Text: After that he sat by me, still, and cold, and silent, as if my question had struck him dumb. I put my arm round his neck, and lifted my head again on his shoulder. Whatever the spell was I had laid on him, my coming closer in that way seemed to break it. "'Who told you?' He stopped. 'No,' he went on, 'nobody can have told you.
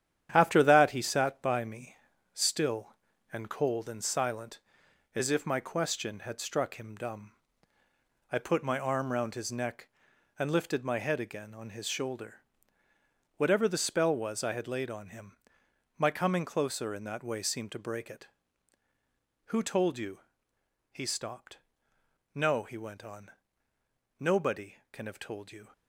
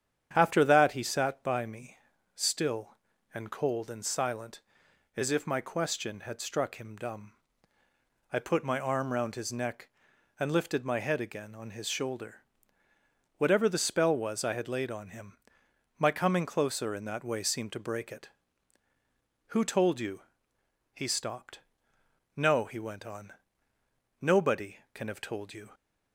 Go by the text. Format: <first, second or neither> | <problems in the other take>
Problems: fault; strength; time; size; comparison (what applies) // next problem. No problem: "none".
second | gets quieter; throughout; 6.5 dB // starts louder than the rest; strong; until 1.3 s; 10 dB; strong in the second